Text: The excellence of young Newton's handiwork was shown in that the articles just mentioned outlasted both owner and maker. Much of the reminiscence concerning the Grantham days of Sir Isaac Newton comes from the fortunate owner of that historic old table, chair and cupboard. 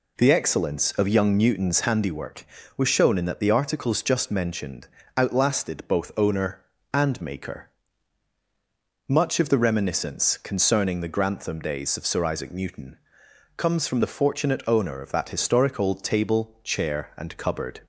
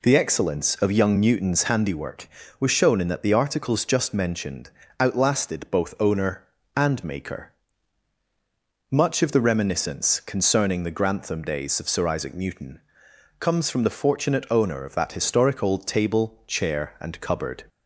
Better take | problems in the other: neither | pauses between "mentioned" and "outlasted"; slight; the same in both // pauses between "Newton" and "comes"; noticeable; the same in both

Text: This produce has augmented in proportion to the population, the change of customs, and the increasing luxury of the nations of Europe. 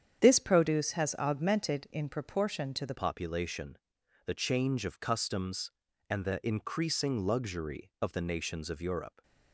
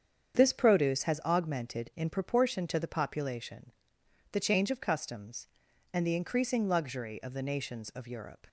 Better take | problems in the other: second | starts louder than the rest; strong; until 1.2 s; 8.5 dB; strong in the second // changes voice at "population"; from 2.9 s on; 6.3 s long

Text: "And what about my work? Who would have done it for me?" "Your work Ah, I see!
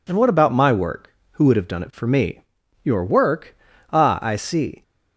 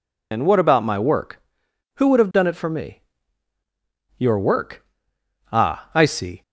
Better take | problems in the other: first | loses the start of "And"; at 0.3 s; 105 ms // pauses between "work" and "Ah"; noticeable; at 4.8 s; 0.66 s long; slight in the first

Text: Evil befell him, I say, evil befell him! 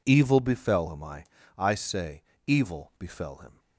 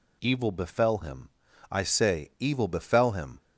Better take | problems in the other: second | says "I" twice; at 1.5 s

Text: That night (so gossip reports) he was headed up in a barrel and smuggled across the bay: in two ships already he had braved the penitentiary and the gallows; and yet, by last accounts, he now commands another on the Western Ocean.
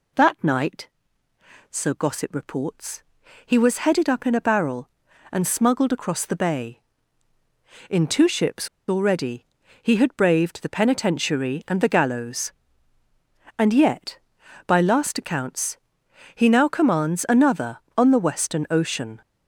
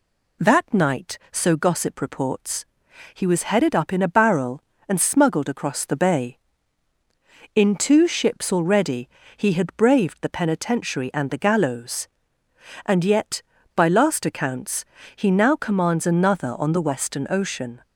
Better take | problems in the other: second | pauses between "ships" and "already"; slight; at 8.6 s; 0.20 s long // pauses between "already" and "he"; at 9.4 s; 0.38 s long; slight in the second

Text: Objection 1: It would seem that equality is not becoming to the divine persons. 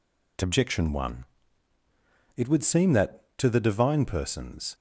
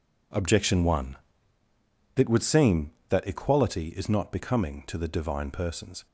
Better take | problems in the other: second | skips "equality is not becoming"; at 3.3 s

